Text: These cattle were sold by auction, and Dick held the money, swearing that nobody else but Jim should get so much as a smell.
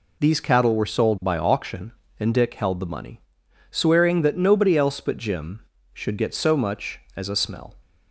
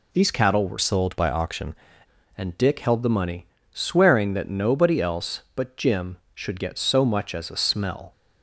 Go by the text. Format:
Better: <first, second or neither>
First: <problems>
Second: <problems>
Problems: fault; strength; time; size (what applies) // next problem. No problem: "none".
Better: first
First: none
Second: changes voice from "sold" to "auction"; from 0.7 to 1.7 s; 1.0 s long